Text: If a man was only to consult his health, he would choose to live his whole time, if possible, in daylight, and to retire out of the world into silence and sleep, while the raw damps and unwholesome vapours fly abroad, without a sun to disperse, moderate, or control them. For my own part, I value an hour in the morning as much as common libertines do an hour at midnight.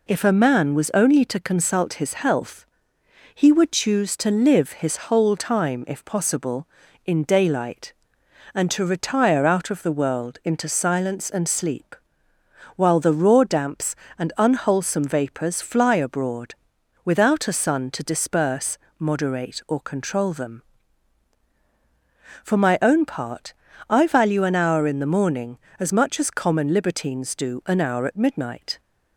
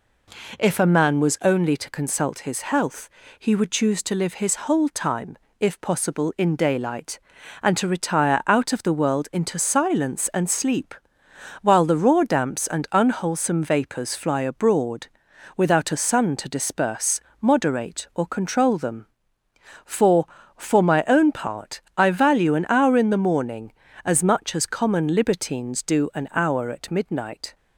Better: first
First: none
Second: says "For" twice; at 20.5 s

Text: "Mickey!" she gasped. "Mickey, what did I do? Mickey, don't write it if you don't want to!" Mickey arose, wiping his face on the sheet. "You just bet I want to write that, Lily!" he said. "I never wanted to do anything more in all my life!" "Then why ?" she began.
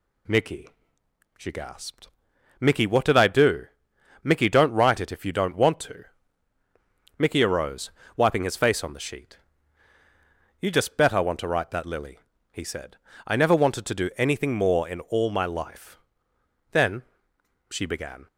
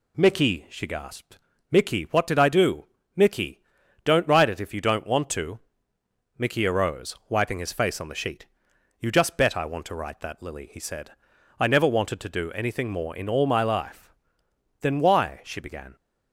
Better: second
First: skips "why"; at 17.1 s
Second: none

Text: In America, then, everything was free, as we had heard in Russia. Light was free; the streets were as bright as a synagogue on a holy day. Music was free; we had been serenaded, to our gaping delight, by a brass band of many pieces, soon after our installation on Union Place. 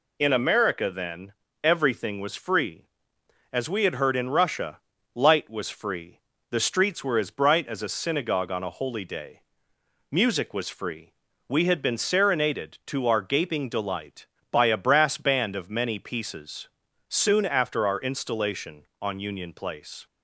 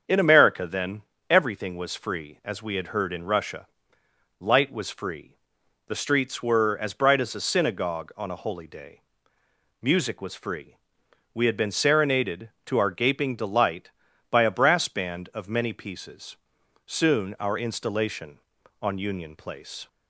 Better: first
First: none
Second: starts louder than the rest; strong; until 1.3 s; 7.5 dB // skips "after"; at 17.3 s

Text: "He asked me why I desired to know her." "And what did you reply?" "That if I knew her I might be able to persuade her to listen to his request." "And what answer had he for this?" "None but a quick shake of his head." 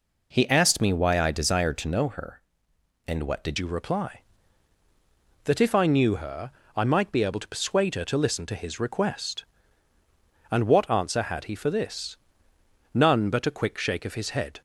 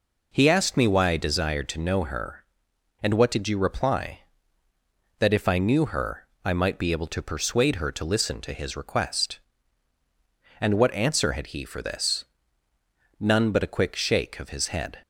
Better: second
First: changes voice at "you"; from 3.5 s on; 11.1 s long // pauses between "her" and "I"; slight; at 6.4 s; 0.26 s long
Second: pauses between "her" and "I"; slight; at 6.2 s; 0.16 s long

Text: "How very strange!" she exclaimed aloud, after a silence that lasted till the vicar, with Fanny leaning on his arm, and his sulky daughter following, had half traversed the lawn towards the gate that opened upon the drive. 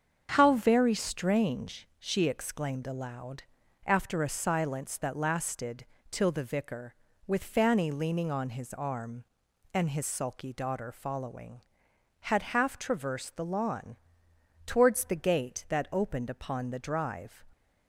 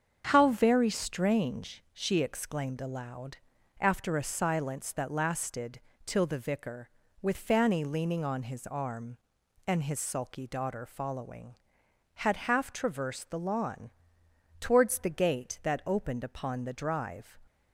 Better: neither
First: starts louder than the rest; strong; until 1.3 s; 7 dB // pauses between "lasted" and "till"; slight; at 5.8 s; 0.24 s long // pauses between "lawn" and "towards"; noticeable; at 13.9 s; 0.70 s long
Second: starts louder than the rest; until 1.3 s; 7 dB // pauses between "lasted" and "till"; slight; at 5.8 s; 0.24 s long // pauses between "lawn" and "towards"; noticeable; at 13.9 s; 0.70 s long

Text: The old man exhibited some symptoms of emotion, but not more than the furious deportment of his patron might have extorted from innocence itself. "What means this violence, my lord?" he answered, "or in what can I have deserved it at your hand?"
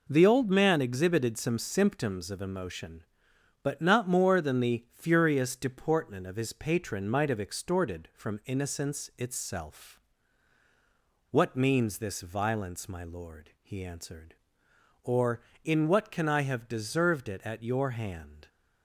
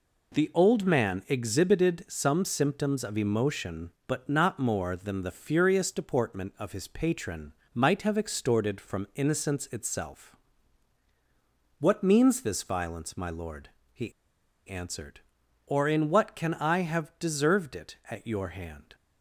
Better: first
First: none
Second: pauses between "patron" and "might"; slight; at 7.5 s; 0.22 s long // pauses between "he" and "answered"; noticeable; at 14.1 s; 0.56 s long

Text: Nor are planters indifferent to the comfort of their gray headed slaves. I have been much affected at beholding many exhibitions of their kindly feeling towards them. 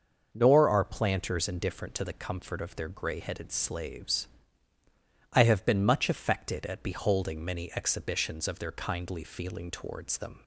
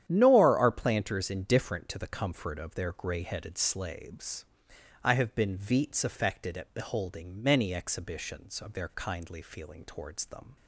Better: first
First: starts louder than the rest; noticeable; until 1.3 s; 6 dB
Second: starts louder than the rest; strong; until 1.0 s; 10 dB // says "veets" for "much"; at 5.5 s

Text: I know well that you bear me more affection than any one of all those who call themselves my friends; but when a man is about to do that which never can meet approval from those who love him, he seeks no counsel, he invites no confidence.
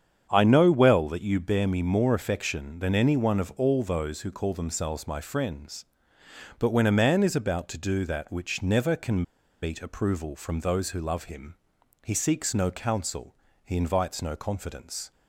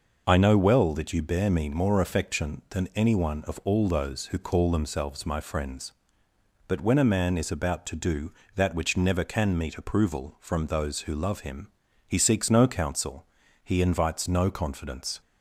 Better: second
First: starts louder than the rest; strong; until 1.3 s; 8 dB // pauses between "can" and "meet"; at 9.2 s; 0.40 s long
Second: none

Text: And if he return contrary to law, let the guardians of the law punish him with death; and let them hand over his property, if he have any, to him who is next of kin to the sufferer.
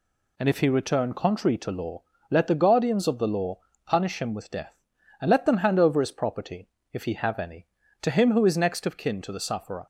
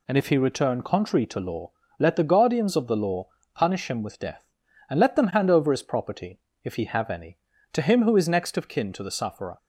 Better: neither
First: pauses between "law" and "punish"; slight; at 3.5 s; 0.26 s long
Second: pauses between "law" and "punish"; slight; at 3.2 s; 0.26 s long

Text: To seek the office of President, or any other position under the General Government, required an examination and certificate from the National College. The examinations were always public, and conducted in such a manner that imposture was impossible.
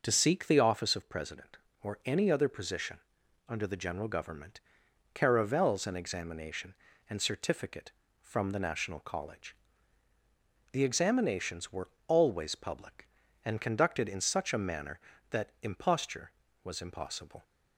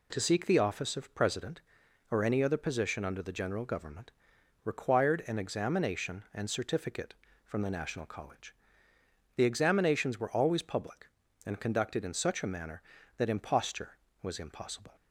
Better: second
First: pauses between "position" and "under"; noticeable; at 2.9 s; 0.50 s long // says "caravels" for "required"; at 5.1 s // pauses between "were" and "always"; slight; at 11.8 s; 0.18 s long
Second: none

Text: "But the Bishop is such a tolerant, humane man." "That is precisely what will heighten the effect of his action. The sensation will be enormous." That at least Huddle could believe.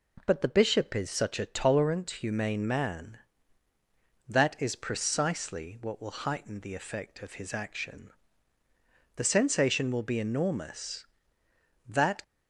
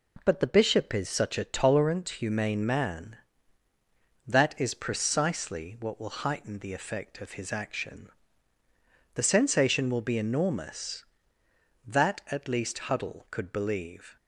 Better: second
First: stops before "at least Huddle could believe"; at 12.2 s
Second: none

